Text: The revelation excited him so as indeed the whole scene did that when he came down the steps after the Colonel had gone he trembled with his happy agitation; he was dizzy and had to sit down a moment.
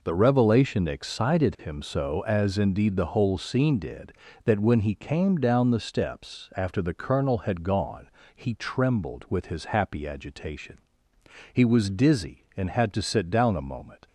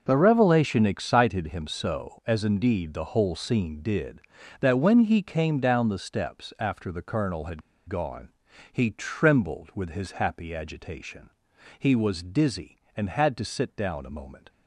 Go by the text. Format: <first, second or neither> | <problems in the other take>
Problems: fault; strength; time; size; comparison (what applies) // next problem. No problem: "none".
first | starts louder than the rest; until 1.0 s; 6 dB // pauses between "had" and "gone"; slight; at 7.6 s; 0.25 s long // pauses between "gone" and "he"; at 8.2 s; 0.44 s long; slight in the first